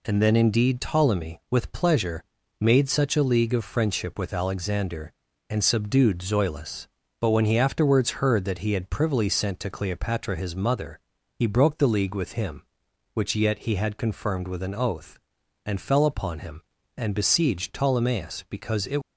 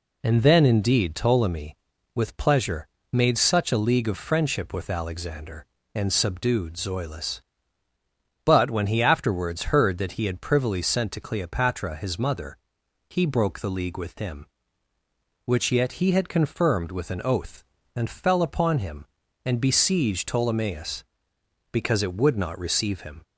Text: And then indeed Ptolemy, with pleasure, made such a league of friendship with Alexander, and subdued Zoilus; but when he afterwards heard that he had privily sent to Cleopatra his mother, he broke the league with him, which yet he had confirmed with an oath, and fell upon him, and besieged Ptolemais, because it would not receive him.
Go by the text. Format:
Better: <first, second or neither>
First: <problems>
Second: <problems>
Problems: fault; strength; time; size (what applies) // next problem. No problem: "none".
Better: second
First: stops before "would not receive him"; at 19.0 s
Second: none